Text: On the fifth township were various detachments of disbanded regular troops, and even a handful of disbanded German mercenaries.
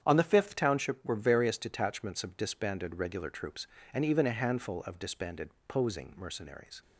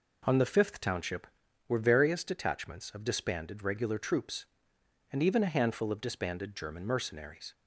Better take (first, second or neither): second